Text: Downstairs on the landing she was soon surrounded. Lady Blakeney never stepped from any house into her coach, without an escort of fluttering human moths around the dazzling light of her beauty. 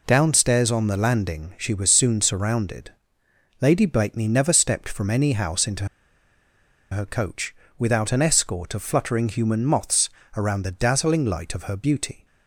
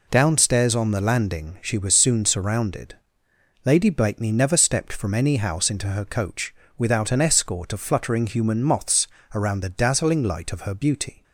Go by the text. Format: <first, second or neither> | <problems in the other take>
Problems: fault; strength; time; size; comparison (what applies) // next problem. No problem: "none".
second | pauses between "into" and "her"; at 5.8 s; 1.0 s long // pauses between "moths" and "around"; slight; at 10.0 s; 0.26 s long; slight in the second